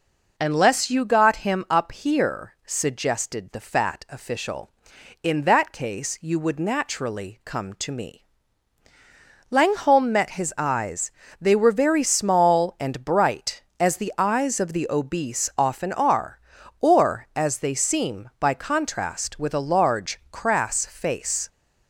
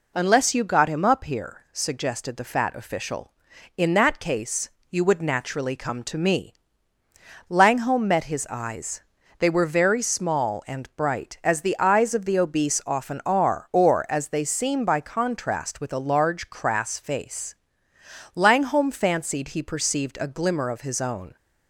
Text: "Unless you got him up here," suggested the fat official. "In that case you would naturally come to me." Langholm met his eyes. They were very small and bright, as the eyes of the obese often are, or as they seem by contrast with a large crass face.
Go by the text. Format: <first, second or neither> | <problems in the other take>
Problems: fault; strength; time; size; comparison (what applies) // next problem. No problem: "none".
first | pauses between "case" and "you"; slight; at 4.6 s; 0.22 s long // goes on to say "Langholm fancied he perceived a glimmer of his own"; strong; from 18.3 s on; 3.0 s long